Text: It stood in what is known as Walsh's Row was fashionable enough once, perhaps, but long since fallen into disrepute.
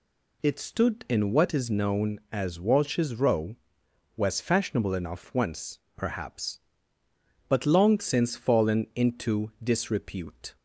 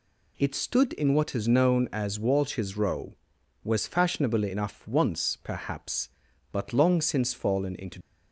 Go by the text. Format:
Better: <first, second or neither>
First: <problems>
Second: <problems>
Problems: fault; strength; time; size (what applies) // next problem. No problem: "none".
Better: first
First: none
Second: stops before "disrepute"; at 8.0 s